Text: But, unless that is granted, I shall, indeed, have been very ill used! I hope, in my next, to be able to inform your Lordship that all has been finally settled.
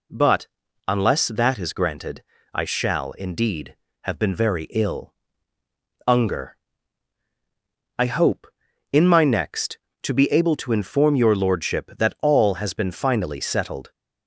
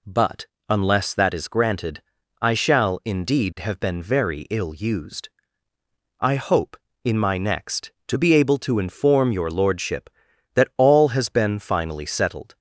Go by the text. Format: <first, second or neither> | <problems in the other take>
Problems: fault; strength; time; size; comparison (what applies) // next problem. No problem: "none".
second | says "unger" for "used"; at 6.0 s